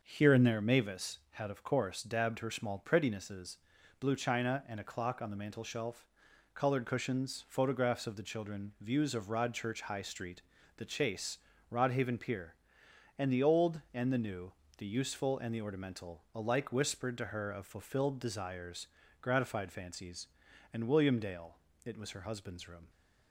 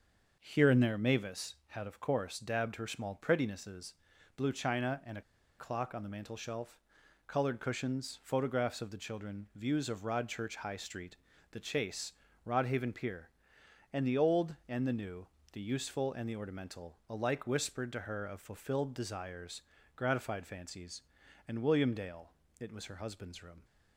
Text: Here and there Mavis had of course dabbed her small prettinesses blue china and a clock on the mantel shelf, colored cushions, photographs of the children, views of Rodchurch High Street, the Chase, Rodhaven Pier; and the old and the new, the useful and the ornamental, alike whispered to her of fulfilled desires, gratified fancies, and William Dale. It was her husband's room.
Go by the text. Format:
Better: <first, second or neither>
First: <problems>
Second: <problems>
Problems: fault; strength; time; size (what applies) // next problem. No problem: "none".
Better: first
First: starts louder than the rest; noticeable; until 1.0 s; 6 dB // pauses between "prettinesses" and "blue"; at 3.5 s; 0.44 s long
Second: starts louder than the rest; noticeable; until 1.3 s; 6 dB // pauses between "prettinesses" and "blue"; at 3.9 s; 0.44 s long // pauses between "a" and "clock"; at 5.2 s; 0.37 s long